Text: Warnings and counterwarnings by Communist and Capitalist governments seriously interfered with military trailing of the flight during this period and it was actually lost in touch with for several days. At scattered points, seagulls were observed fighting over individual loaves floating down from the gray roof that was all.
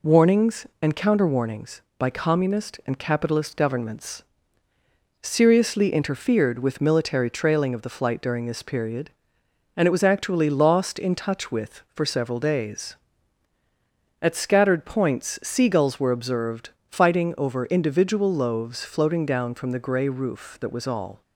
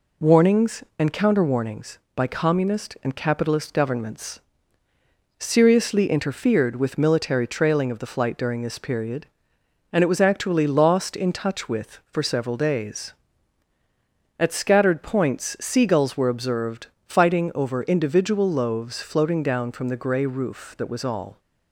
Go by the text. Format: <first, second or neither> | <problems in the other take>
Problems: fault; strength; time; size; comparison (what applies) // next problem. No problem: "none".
neither | pauses between "governments" and "seriously"; noticeable; the same in both // pauses between "observed" and "fighting"; slight; the same in both